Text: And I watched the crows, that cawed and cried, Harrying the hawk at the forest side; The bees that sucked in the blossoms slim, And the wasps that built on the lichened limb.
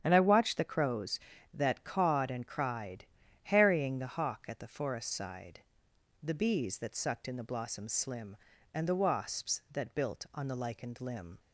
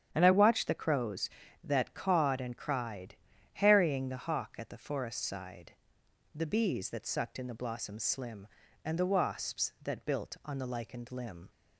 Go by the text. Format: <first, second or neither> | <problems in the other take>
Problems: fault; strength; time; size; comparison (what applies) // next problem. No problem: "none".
neither | starts louder than the rest; strong; the same in both